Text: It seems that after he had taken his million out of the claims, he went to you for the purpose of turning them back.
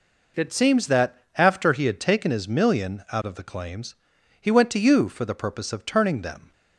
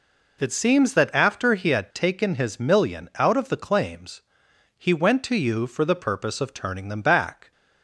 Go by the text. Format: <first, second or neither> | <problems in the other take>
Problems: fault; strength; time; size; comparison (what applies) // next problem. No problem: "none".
second | pauses between "that" and "after"; slight; at 1.1 s; 0.20 s long // stops before "back"; at 6.5 s